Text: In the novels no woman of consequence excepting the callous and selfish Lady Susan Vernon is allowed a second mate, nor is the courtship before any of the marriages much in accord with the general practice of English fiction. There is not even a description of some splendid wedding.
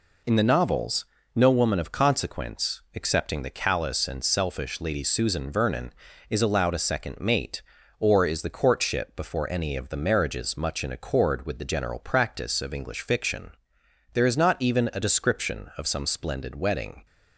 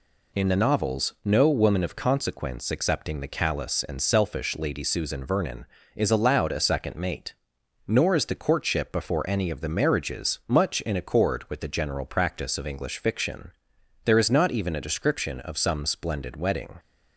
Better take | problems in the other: second | pauses between "novels" and "no"; slight; at 1.0 s; 0.30 s long // says "or" for "nor"; at 7.9 s

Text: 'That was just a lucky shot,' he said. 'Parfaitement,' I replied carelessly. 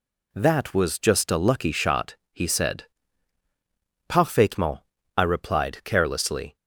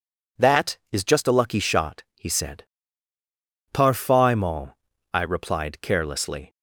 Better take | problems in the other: first | says "is" for "was"; at 0.9 s

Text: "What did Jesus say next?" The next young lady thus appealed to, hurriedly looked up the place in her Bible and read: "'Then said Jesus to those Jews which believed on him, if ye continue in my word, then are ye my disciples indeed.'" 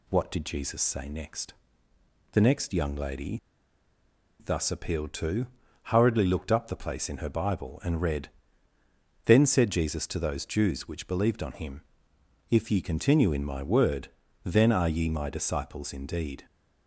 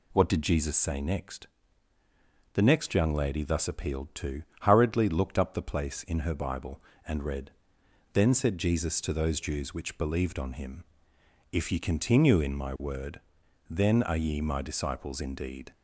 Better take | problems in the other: second | pauses between "lady" and "thus"; at 3.3 s; 1.0 s long

